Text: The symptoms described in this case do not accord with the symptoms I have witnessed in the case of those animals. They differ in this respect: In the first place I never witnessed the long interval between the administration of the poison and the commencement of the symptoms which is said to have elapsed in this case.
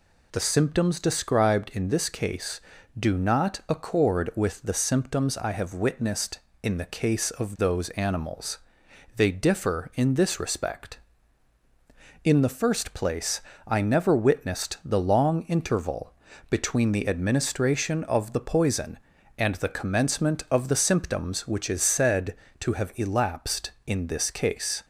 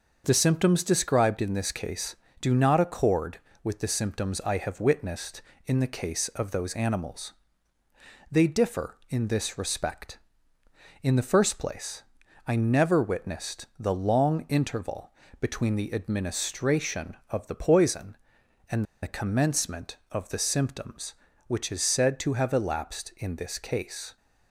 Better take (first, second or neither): first